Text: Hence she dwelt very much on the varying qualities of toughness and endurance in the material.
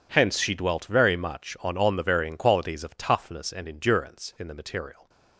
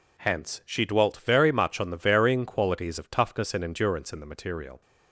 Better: second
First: says "on" twice; at 1.7 s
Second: none

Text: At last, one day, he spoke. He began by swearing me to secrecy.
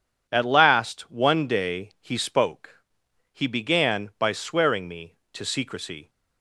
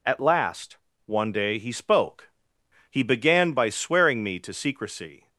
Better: neither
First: none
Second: none

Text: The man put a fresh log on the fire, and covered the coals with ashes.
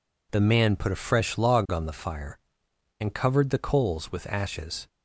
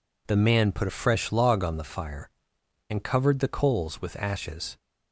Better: neither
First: none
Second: none

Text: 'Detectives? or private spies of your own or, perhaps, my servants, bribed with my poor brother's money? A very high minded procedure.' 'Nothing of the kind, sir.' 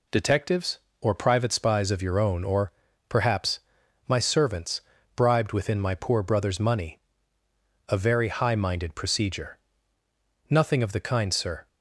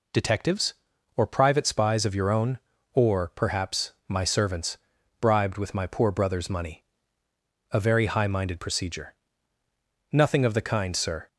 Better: second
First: says "within" for "with"; at 5.5 s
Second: none

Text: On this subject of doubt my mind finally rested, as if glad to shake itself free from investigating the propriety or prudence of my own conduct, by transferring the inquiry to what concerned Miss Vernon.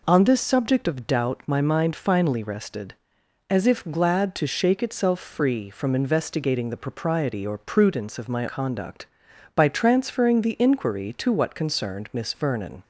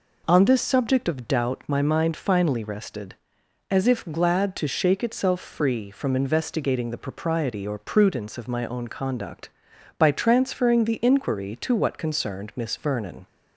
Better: second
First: skips "own"; at 8.4 s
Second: none

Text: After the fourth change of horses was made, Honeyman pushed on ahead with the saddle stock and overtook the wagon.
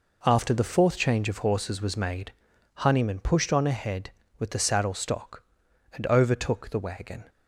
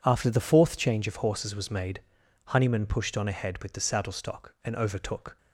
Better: first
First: none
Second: stops before "the wagon"; at 5.3 s

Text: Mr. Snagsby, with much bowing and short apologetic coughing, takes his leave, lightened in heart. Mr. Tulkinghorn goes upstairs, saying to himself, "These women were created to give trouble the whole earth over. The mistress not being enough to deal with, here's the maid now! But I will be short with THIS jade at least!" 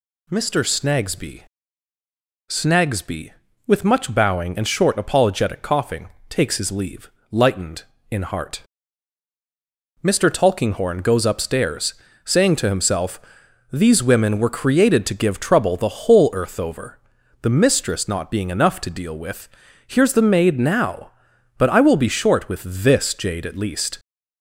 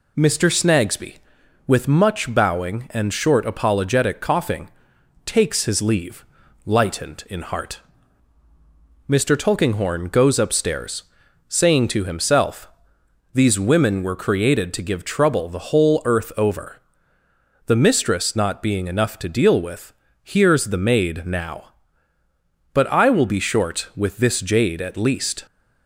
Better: second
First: says "Snagsby" twice; at 2.4 s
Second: none

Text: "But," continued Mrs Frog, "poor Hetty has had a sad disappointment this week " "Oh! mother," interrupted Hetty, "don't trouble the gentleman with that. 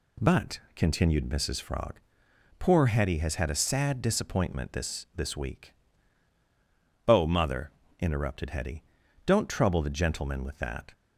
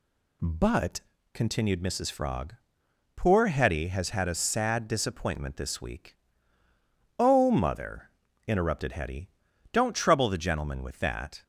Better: second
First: says "this" twice; at 5.1 s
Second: none

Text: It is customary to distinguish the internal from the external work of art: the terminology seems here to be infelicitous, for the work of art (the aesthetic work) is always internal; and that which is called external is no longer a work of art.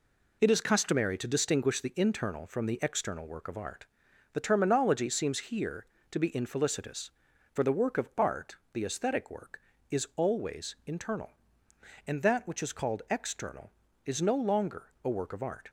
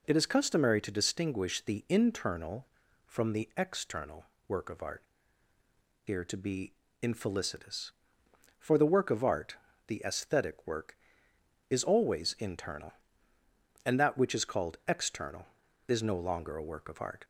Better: first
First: none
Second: pauses between "external" and "work"; slight; at 4.2 s; 0.24 s long // skips "the terminology seems"; at 5.5 s // pauses between "be" and "infelicitous"; slight; at 6.7 s; 0.26 s long

